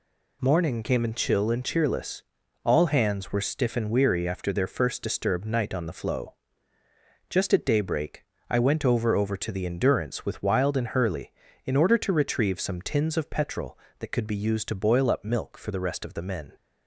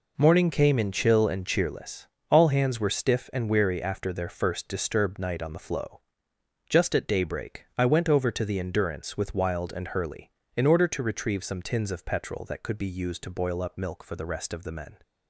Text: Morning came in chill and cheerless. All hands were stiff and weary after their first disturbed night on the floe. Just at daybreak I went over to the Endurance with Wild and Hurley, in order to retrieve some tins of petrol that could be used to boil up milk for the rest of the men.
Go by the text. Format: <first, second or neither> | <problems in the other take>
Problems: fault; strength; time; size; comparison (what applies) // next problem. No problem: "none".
second | pauses between "daybreak" and "I"; slight; at 8.2 s; 0.24 s long // says "over" twice; at 9.1 s